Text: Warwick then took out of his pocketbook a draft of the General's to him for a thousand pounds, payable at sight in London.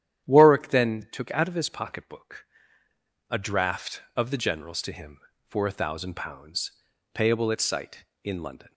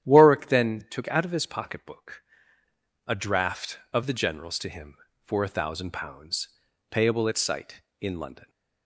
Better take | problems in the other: neither | starts louder than the rest; strong; the same in both // pauses between "pocketbook" and "a"; noticeable; the same in both

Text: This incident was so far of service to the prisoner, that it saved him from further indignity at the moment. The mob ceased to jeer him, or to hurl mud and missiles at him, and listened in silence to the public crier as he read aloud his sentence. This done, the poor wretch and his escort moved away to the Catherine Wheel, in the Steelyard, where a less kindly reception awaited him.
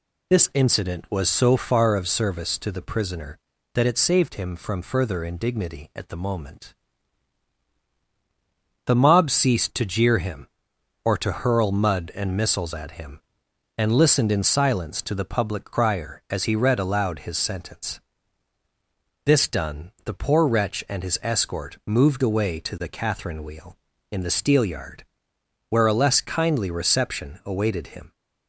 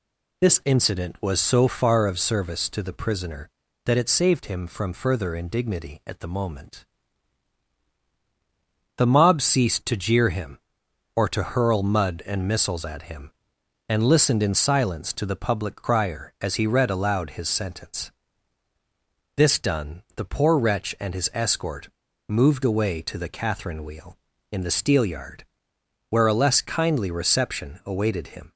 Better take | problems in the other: first | pauses between "escort" and "moved"; at 21.8 s; 0.40 s long

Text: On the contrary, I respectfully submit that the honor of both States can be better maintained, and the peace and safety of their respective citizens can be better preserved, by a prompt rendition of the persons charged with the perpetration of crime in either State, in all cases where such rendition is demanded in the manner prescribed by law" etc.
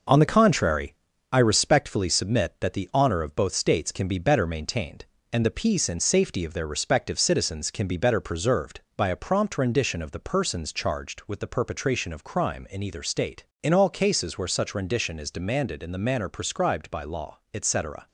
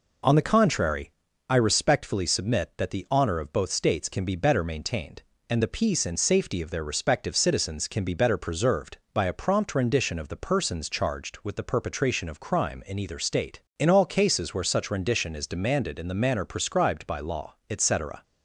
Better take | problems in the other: second | gets quieter; throughout; 6 dB

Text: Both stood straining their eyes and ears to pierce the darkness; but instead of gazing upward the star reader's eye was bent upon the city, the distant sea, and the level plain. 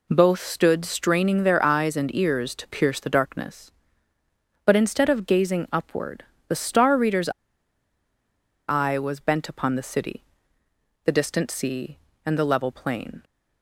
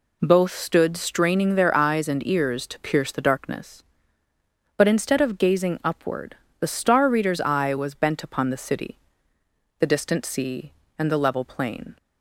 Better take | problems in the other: second | pauses between "upward" and "the"; slight; at 6.2 s; 0.24 s long; slight in the second // pauses between "reader's" and "eye"; strong; at 7.2 s; 1.4 s long

